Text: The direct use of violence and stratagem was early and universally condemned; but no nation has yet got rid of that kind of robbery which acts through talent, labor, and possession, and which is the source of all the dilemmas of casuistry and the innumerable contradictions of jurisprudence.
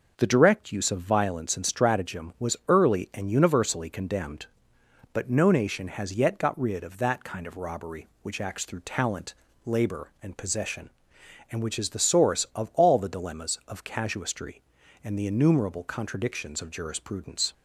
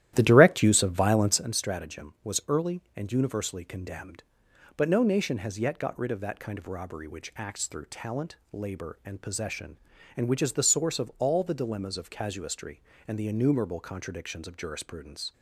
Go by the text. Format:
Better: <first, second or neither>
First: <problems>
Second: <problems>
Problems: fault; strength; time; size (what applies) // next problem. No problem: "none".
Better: first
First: none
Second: starts louder than the rest; strong; until 1.5 s; 13 dB